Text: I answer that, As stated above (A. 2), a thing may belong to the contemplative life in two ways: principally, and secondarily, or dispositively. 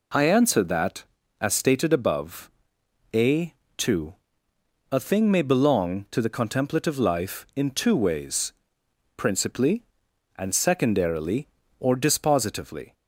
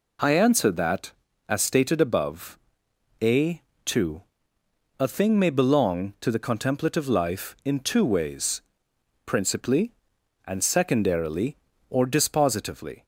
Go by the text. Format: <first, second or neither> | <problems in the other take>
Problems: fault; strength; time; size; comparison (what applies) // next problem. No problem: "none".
neither | none